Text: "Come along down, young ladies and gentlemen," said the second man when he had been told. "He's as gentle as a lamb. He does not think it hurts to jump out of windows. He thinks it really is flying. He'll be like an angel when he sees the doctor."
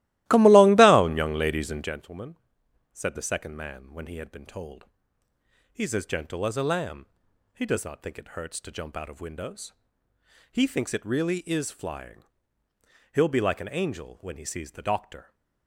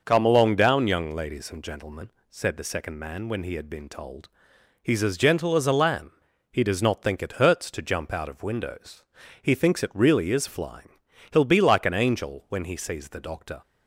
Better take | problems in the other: second | starts louder than the rest; strong; until 2.0 s; 16.5 dB

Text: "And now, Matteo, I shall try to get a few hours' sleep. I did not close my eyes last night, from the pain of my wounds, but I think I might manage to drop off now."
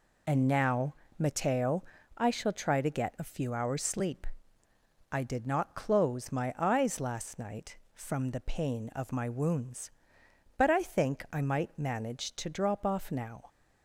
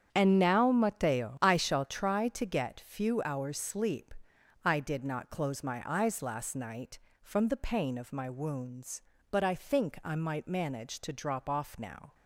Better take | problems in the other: first | starts louder than the rest; strong; until 1.1 s; 8 dB // skips "a"; at 2.8 s

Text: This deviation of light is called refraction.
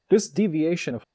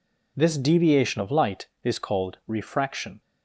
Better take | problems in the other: second | stops before "light is called refraction"; at 1.0 s

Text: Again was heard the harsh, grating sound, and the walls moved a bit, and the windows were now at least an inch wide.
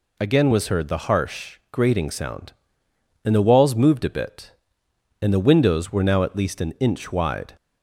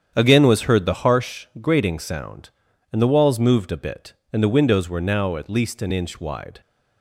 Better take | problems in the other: first | starts louder than the rest; strong; until 1.4 s; 8.5 dB

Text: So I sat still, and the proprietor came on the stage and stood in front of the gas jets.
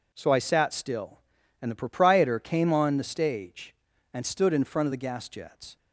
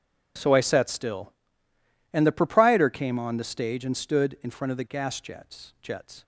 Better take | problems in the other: first | says "jets" twice; at 5.8 s

